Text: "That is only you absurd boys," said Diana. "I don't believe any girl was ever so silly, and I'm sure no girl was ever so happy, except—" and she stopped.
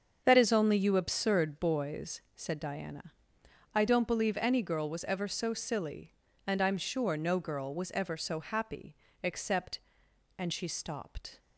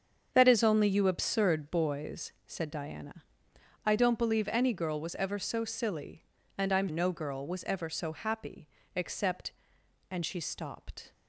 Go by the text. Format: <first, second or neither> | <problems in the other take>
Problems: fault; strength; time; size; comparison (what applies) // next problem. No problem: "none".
first | starts louder than the rest; strong; until 1.3 s; 7 dB; also in the first // skips "sure"; at 6.8 s